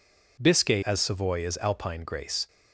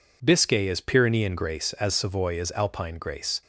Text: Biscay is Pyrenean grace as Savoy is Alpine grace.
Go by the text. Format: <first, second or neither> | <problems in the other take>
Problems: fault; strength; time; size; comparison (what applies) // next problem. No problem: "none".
second | skips "is Pyrenean grace"; at 0.8 s